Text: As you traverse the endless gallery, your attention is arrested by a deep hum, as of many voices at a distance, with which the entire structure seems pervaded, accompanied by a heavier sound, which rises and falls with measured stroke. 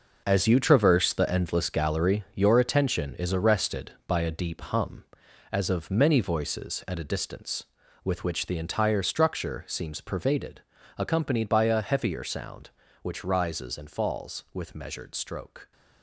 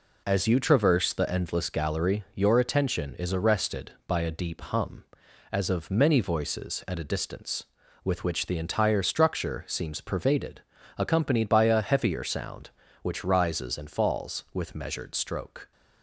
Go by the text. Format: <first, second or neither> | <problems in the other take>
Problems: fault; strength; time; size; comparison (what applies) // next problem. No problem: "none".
second | gets quieter; strong; throughout; 10.5 dB